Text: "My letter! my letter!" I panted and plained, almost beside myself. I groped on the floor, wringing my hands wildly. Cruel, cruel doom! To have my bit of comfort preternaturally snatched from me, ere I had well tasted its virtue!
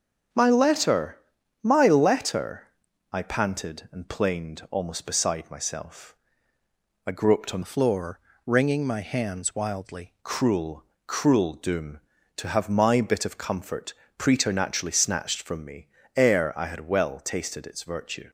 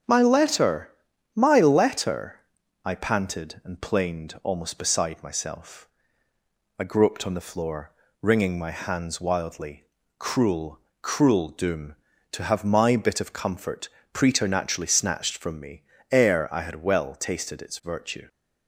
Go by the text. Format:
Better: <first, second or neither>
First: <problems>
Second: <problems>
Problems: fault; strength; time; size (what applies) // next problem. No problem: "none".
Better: second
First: starts louder than the rest; until 1.7 s; 6.5 dB // changes voice from "the" to "wildly"; from 7.6 to 10.1 s; 2.5 s long // pauses between "comfort" and "preternaturally"; slight; at 13.9 s; 0.24 s long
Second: starts louder than the rest; until 1.4 s; 7 dB // pauses between "comfort" and "preternaturally"; slight; at 13.8 s; 0.24 s long